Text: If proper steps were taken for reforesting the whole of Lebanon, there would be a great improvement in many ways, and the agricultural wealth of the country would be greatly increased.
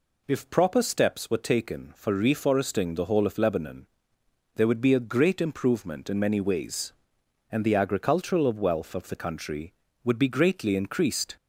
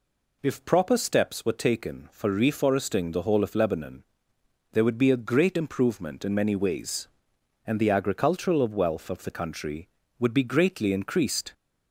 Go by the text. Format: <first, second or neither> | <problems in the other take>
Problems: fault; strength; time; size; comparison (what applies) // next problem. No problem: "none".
neither | none